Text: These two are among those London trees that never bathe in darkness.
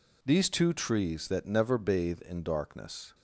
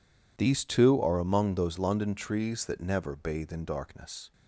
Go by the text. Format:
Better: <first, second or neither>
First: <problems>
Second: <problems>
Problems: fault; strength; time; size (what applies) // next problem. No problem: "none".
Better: second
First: skips "are among those London"; at 0.7 s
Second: none